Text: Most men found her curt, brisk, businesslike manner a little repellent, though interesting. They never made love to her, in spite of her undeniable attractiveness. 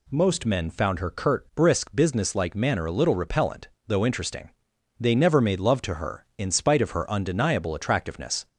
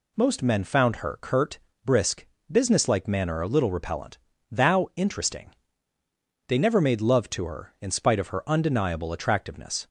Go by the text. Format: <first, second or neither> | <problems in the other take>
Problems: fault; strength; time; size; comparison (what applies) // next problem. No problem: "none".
first | says "thou" for "though"; at 4.4 s